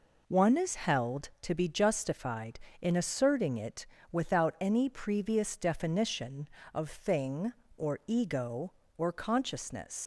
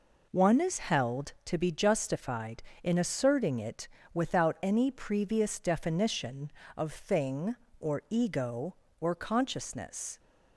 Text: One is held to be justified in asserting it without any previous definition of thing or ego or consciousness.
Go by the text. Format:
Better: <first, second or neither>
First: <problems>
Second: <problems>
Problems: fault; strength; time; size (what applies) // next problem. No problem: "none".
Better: second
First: pauses between "it" and "without"; slight; at 3.8 s; 0.26 s long // leaves "consciousness" unfinished; at 10.0 s; 105 ms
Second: pauses between "it" and "without"; slight; at 3.8 s; 0.26 s long